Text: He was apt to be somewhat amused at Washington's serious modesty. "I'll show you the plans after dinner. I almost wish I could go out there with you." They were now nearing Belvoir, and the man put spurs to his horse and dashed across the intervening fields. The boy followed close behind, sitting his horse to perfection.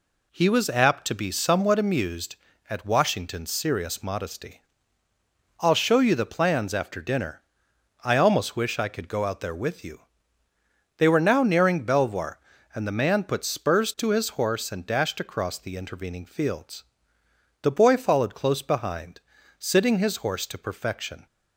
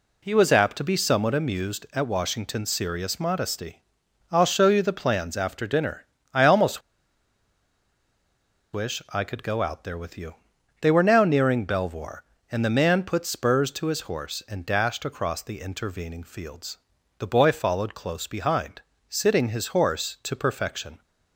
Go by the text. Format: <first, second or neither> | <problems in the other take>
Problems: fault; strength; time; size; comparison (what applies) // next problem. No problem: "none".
first | pauses between "almost" and "wish"; strong; at 6.7 s; 1.9 s long